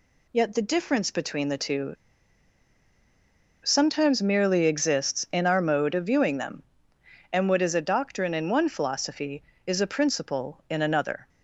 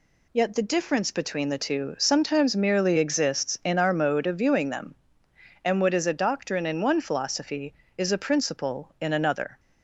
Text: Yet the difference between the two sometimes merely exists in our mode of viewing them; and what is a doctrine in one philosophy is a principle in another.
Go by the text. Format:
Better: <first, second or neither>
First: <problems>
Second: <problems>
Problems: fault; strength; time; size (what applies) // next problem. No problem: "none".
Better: second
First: pauses between "two" and "sometimes"; strong; at 1.9 s; 1.6 s long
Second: none